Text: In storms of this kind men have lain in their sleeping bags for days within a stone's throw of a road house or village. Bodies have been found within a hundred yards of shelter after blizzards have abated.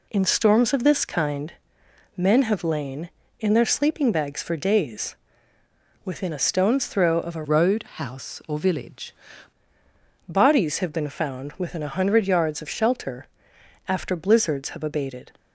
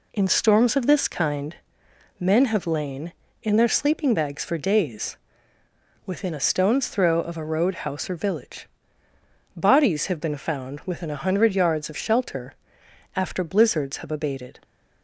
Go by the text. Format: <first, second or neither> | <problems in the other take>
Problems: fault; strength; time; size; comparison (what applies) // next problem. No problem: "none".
second | pauses between "kind" and "men"; noticeable; at 1.5 s; 0.62 s long; noticeable in the second // pauses between "days" and "within"; noticeable; at 5.1 s; 0.88 s long; noticeable in the second // changes voice from "road" to "village"; from 7.4 to 9.1 s; 1.7 s long // pauses between "shelter" and "after"; noticeable; at 13.2 s; 0.62 s long; noticeable in the second